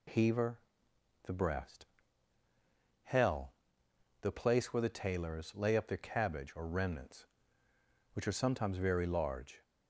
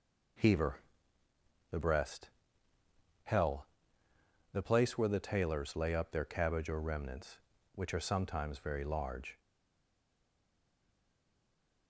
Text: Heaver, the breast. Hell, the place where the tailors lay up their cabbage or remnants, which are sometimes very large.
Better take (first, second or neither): first